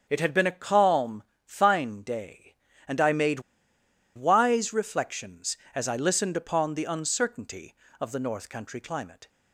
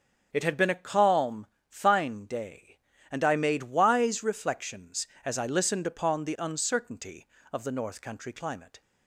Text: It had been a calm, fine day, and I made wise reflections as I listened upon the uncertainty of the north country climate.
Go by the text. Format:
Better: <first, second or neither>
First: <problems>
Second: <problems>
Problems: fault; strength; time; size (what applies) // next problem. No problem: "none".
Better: second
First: starts louder than the rest; strong; until 1.1 s; 7.5 dB // pauses between "made" and "wise"; noticeable; at 3.3 s; 0.76 s long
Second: starts louder than the rest; until 1.3 s; 7 dB